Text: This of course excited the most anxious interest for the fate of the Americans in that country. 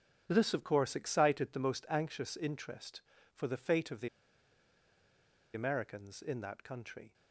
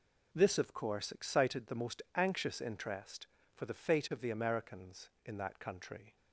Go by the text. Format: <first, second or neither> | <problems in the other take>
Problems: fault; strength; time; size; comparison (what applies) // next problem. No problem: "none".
second | starts louder than the rest; strong; until 1.2 s; 8 dB // pauses between "the" and "Americans"; strong; at 4.0 s; 1.4 s long